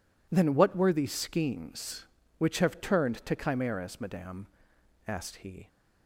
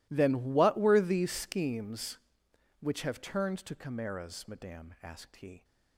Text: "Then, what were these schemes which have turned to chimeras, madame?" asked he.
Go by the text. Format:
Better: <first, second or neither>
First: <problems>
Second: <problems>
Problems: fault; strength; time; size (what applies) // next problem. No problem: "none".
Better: neither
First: none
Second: none